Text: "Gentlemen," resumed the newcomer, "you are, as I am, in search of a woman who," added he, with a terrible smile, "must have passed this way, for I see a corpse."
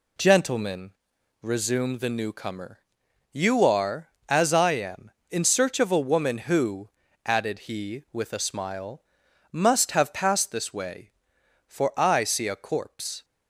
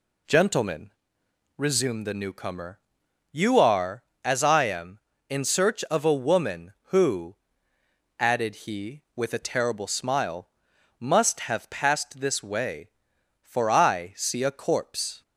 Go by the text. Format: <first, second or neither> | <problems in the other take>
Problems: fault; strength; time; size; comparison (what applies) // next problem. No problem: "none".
second | skips "terrible"; at 8.3 s